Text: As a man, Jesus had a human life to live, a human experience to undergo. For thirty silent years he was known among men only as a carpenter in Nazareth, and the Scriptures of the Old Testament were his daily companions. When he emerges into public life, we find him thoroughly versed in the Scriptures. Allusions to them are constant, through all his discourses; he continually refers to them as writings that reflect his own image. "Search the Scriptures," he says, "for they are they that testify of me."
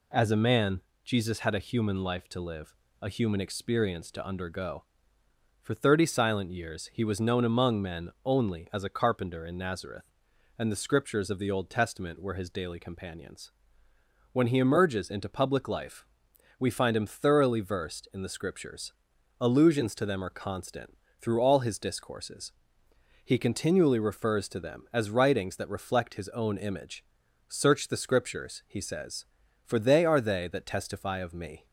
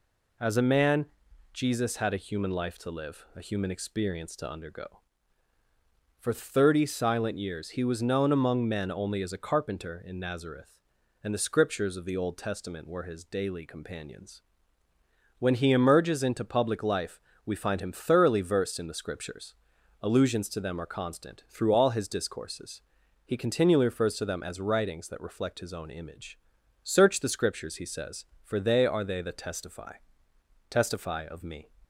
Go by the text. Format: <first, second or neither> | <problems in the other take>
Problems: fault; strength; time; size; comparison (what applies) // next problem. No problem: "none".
first | says "testify" twice; at 30.6 s